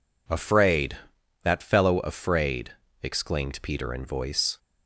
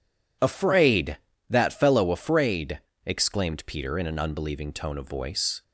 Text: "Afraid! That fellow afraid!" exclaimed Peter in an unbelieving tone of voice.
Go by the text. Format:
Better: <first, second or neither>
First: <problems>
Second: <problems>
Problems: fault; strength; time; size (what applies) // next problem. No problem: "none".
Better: second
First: skips "an unbelieving tone of"; at 4.0 s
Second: none